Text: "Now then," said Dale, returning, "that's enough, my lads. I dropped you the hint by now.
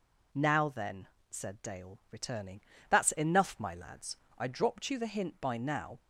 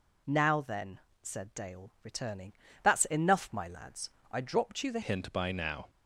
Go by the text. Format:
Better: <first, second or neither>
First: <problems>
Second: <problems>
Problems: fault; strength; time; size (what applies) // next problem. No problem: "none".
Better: first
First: none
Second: changes voice at "hint"; from 5.0 s on; 0.8 s long